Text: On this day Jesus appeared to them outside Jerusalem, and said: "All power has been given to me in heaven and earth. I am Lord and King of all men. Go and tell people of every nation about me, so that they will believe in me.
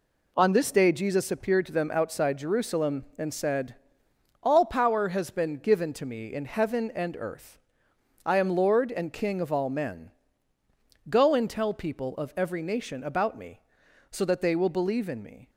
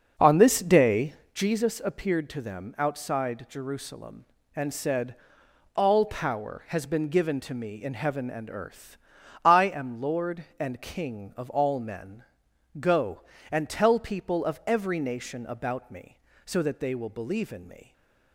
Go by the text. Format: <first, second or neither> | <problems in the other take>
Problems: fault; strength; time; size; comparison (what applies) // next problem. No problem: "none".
first | starts louder than the rest; noticeable; until 1.5 s; 6 dB // pauses between "day" and "Jesus"; slight; at 1.1 s; 0.22 s long // stays silent after the last word; slight; from 17.8 s on; 0.5 s long